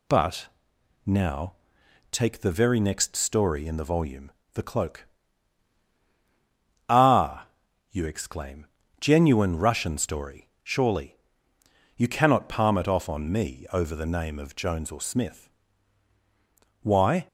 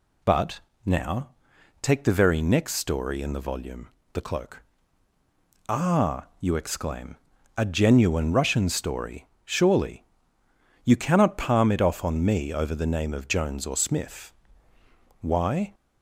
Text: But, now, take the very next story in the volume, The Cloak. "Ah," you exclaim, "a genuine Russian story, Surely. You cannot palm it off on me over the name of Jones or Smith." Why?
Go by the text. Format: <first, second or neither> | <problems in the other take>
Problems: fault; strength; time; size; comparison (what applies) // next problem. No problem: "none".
second | skips "a"; at 8.8 s